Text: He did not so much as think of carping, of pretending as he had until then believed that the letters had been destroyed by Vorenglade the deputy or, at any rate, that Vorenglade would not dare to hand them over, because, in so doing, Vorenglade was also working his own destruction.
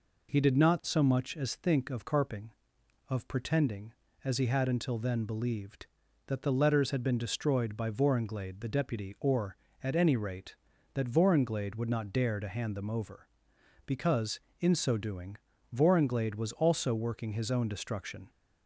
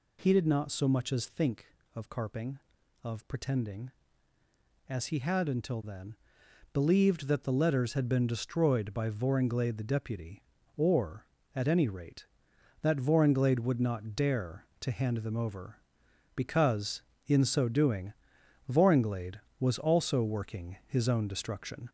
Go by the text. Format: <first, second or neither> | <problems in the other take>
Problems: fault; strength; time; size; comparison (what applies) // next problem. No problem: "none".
first | gets louder; slight; throughout; 3 dB // pauses between "then" and "believed"; noticeable; at 6.1 s; 0.60 s long